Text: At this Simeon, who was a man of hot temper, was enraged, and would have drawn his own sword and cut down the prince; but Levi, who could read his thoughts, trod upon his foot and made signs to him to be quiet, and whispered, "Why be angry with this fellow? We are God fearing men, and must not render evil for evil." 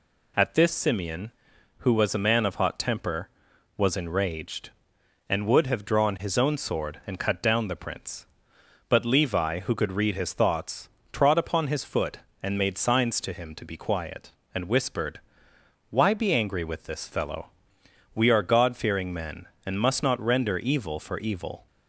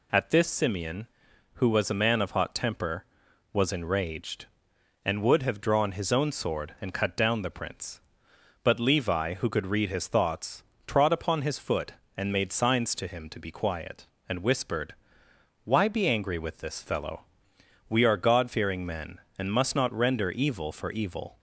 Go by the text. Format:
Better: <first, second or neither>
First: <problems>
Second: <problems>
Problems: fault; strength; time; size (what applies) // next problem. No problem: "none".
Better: neither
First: none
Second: none